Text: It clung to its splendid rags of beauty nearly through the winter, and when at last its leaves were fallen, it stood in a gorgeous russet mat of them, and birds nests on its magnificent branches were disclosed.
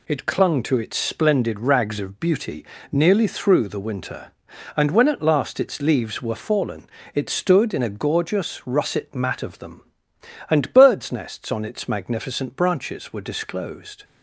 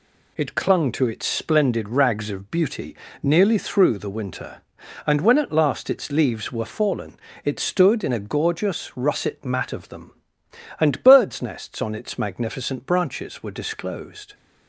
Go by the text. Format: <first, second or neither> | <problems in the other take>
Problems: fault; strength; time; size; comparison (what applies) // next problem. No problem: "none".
neither | pauses between "beauty" and "nearly"; slight; the same in both